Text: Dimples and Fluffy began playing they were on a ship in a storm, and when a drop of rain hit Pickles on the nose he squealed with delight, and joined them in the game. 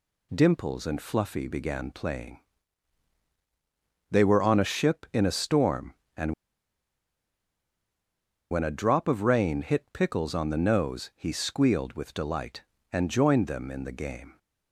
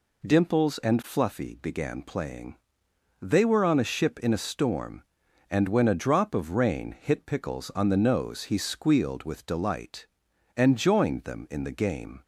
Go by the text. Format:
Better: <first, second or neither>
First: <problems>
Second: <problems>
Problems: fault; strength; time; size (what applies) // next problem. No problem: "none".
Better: second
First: pauses between "playing" and "they"; strong; at 2.3 s; 1.7 s long // pauses between "and" and "when"; strong; at 6.3 s; 2.1 s long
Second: pauses between "playing" and "they"; noticeable; at 2.5 s; 0.66 s long